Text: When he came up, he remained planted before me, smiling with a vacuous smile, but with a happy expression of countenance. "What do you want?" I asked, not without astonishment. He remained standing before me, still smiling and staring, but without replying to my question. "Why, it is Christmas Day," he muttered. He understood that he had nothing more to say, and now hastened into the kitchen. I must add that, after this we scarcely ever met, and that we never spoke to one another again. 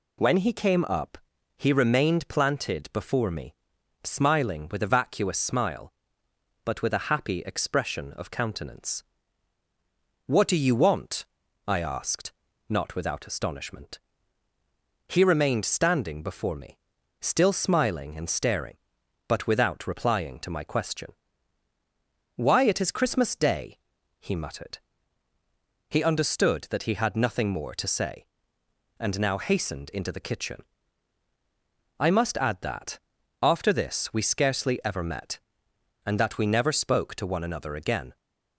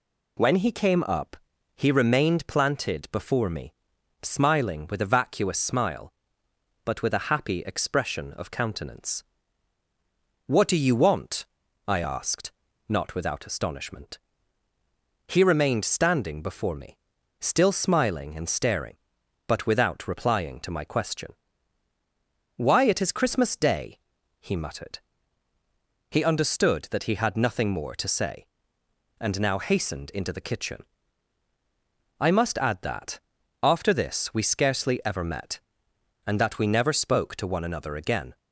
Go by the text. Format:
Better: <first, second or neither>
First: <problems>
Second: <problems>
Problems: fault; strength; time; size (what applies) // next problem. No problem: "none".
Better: neither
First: none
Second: none